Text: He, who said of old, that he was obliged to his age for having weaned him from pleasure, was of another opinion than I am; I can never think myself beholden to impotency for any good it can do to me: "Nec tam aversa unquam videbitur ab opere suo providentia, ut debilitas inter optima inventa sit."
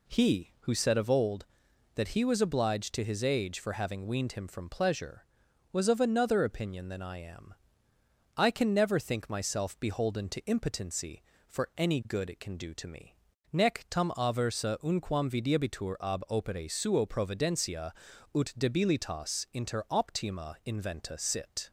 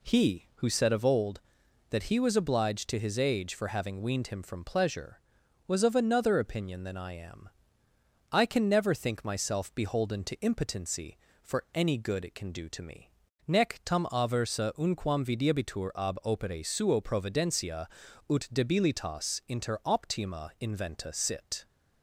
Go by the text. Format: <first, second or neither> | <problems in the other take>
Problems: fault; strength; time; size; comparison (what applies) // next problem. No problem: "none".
neither | none